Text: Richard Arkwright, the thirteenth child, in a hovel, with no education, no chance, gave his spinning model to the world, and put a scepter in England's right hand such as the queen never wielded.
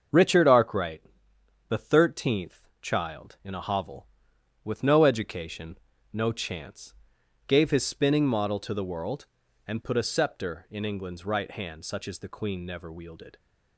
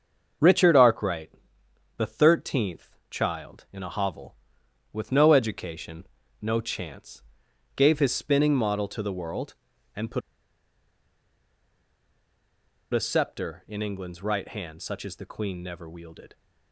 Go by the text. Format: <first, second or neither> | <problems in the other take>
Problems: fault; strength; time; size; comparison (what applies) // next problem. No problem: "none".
first | starts louder than the rest; until 2.0 s; 6.5 dB; also in the first // pauses between "put" and "a"; strong; at 10.2 s; 2.7 s long